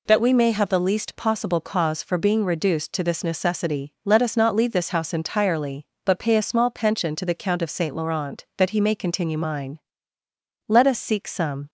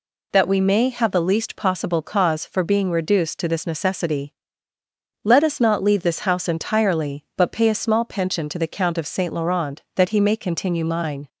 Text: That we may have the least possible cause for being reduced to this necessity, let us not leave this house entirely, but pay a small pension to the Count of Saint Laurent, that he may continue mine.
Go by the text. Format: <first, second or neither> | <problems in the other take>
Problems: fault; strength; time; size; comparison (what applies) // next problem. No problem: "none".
second | goes on to say "Let us seek some"; noticeable; from 10.6 s on; 1.0 s long